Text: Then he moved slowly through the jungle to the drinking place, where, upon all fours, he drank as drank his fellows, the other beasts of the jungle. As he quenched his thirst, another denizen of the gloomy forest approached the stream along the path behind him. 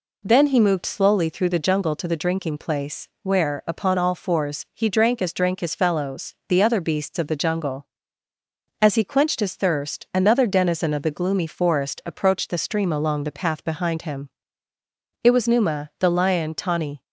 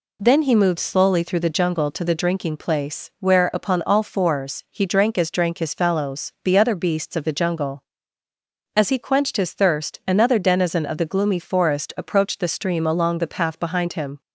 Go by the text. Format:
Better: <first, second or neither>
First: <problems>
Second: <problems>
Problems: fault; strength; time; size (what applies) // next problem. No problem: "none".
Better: second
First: goes on to say "It was Numa the lion tawny"; strong; from 15.2 s on; 1.7 s long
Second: none